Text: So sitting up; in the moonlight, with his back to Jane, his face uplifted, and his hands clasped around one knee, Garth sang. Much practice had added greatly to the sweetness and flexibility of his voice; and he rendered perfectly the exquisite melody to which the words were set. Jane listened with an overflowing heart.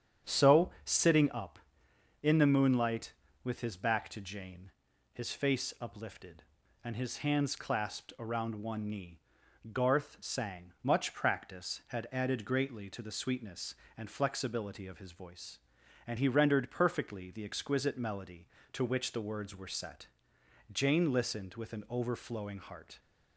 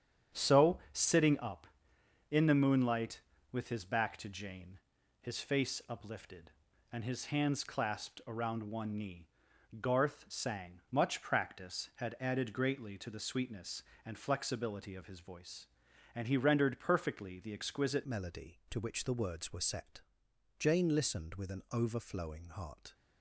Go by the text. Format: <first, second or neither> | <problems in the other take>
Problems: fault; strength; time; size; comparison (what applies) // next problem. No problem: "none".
first | starts louder than the rest; strong; until 1.4 s; 8.5 dB; strong in the first // changes voice at "melody"; from 18.0 s on; 4.9 s long